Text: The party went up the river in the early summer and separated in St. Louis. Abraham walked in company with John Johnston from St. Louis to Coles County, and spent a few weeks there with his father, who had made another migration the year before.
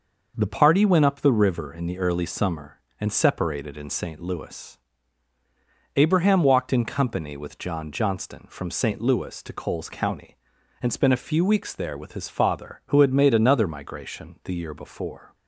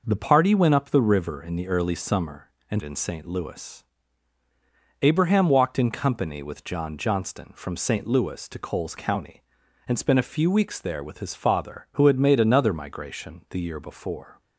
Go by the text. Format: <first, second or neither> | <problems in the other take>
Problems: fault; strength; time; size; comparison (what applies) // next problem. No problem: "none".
first | skips "separated"; at 2.8 s